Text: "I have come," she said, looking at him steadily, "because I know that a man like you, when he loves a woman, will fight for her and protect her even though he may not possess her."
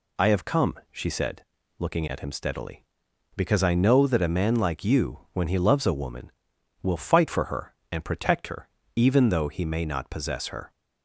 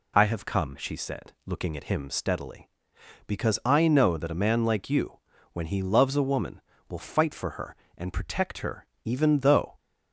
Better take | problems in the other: first | pauses between "her" and "even"; slight; at 8.8 s; 0.18 s long; slight in the first // stops before "he may not possess her"; at 9.7 s

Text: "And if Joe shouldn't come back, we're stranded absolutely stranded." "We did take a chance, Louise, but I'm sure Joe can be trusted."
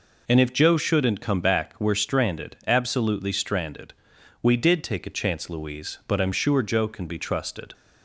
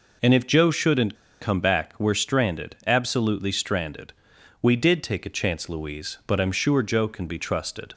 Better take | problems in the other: first | pauses between "shouldn't" and "come"; slight; at 1.1 s; 0.25 s long

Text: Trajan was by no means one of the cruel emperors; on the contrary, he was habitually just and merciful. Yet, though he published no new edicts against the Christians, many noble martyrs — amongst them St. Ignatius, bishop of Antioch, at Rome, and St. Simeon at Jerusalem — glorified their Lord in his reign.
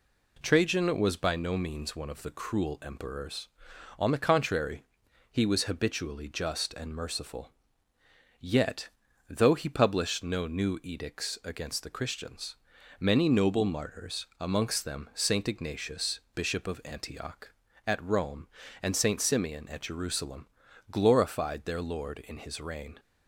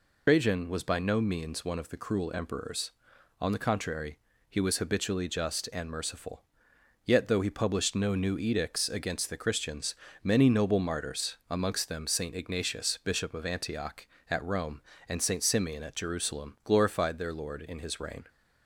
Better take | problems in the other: first | loses the start of "Trajan"; at 0.2 s; 100 ms

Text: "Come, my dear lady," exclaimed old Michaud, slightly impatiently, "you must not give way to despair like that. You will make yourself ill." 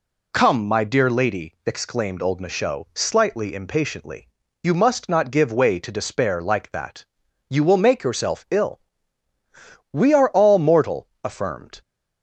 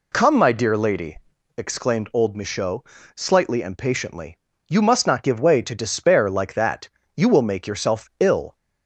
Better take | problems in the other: second | goes on to say "We are all mortal affirmed"; strong; from 9.9 s on; 1.9 s long

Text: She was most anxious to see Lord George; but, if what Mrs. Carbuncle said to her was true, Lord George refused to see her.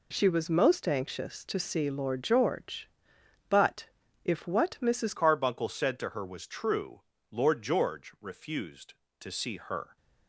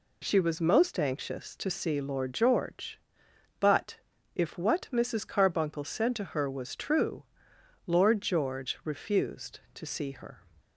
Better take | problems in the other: second | changes voice at "Carbuncle"; from 5.1 s on; 4.8 s long

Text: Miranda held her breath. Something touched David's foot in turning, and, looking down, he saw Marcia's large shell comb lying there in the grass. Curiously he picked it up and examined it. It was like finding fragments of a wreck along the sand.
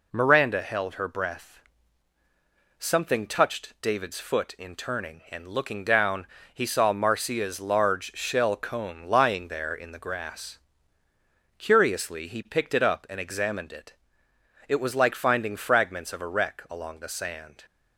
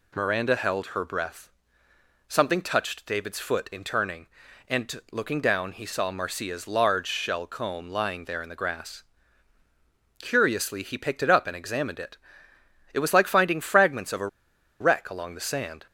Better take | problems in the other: first | pauses between "a" and "wreck"; noticeable; at 14.2 s; 0.52 s long

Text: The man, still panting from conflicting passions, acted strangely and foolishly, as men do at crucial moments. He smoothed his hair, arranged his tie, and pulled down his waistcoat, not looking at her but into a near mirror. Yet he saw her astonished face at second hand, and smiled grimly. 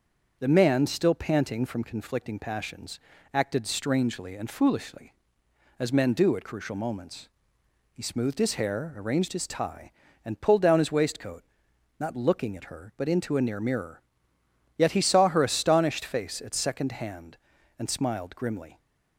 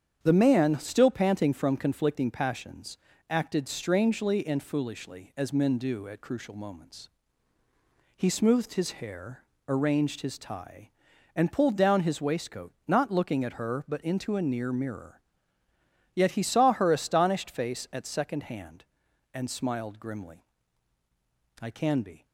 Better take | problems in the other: first | starts louder than the rest; strong; until 1.2 s; 8 dB; also in the first // goes on to say "I can be"; noticeable; from 21.5 s on; 0.66 s long

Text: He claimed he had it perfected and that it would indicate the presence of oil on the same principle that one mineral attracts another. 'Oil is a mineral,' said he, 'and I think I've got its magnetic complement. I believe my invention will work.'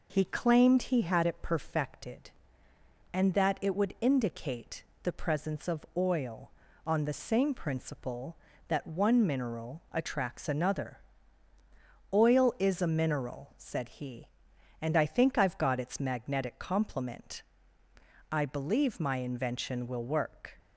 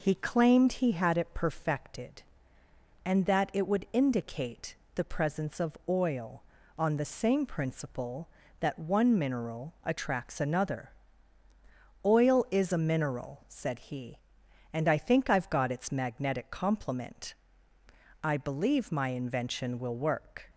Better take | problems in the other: neither | pauses between "indicate" and "the"; slight; the same in both

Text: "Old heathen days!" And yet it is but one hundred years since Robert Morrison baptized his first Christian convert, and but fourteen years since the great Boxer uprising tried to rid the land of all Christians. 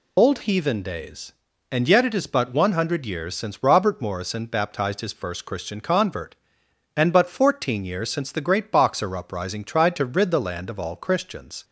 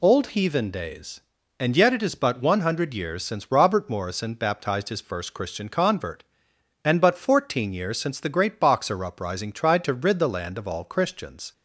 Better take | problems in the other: second | loses the start of "Old"; at 0.1 s; 35 ms

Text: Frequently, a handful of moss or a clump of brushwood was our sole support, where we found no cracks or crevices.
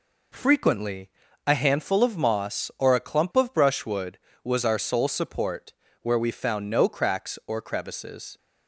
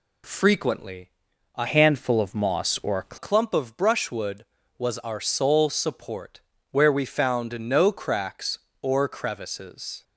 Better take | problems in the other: first | changes voice from "handful" to "a"; from 1.6 to 3.1 s; 1.5 s long

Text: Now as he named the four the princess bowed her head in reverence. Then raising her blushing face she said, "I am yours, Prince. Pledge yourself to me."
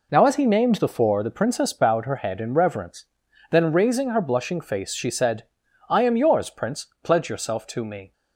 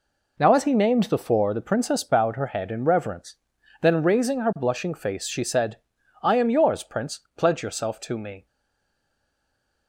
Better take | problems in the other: first | stays silent after the last word; noticeable; from 8.4 s on; 1.4 s long

